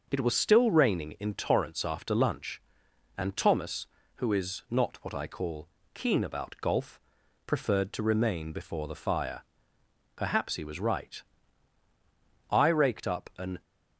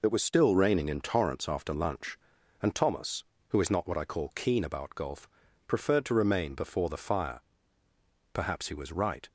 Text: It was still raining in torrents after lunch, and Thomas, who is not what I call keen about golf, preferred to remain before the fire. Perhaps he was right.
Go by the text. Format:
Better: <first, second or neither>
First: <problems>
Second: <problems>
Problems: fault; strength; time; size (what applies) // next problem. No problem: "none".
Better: second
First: pauses between "call" and "keen"; slight; at 5.6 s; 0.26 s long // goes on to say "I raked up an"; noticeable; from 12.5 s on; 1.0 s long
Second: none